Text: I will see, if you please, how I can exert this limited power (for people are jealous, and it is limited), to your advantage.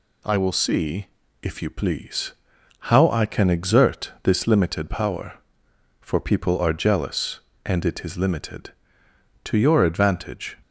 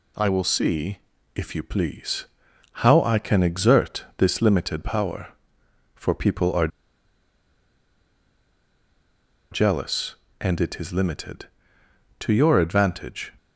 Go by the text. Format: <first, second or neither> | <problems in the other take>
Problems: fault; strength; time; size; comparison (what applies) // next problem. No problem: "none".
first | pauses between "are" and "jealous"; strong; at 6.6 s; 2.8 s long